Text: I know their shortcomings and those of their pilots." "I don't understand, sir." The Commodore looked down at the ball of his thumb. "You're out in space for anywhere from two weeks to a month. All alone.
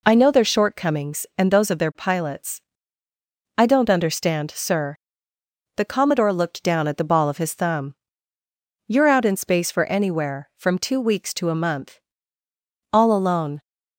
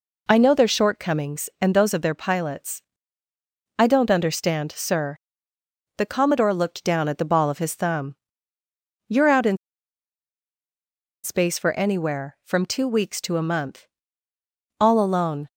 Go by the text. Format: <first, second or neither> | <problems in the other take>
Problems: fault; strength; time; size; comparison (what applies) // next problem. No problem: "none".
first | pauses between "in" and "space"; strong; at 9.5 s; 1.6 s long